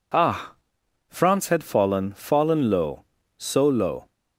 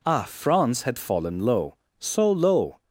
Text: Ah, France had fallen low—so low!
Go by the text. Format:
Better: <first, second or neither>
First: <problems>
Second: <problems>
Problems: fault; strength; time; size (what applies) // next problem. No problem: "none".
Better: second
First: says "fallen" twice; at 2.1 s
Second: none